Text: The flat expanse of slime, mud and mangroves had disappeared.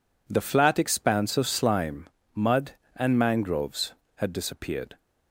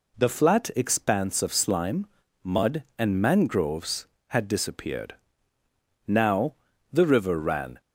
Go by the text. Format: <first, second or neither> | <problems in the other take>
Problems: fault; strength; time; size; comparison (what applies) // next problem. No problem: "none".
first | goes on to say "Now the river ran"; strong; from 6.0 s on; 1.7 s long